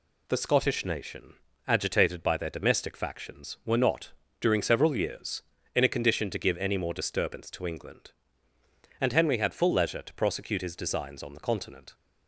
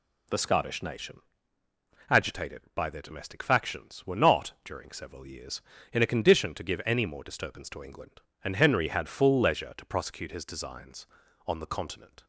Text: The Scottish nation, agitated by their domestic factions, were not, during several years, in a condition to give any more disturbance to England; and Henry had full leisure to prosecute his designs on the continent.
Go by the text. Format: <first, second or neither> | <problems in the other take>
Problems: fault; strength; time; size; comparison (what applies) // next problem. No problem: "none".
neither | none